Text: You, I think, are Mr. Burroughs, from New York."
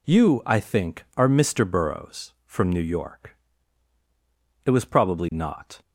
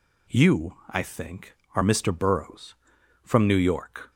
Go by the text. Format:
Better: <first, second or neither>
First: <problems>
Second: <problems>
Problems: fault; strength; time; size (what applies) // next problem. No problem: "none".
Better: second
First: goes on to say "It was probably not"; noticeable; from 4.6 s on; 1.1 s long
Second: none